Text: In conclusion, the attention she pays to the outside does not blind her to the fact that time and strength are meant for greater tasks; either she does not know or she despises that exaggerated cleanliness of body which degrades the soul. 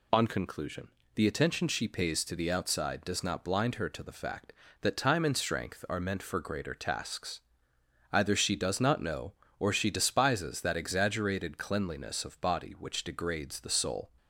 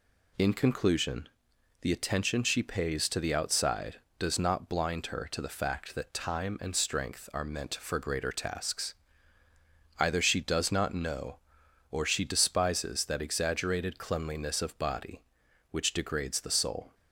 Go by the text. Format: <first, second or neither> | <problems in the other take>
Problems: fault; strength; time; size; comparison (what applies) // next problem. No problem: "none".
second | says "On" for "In"; at 0.1 s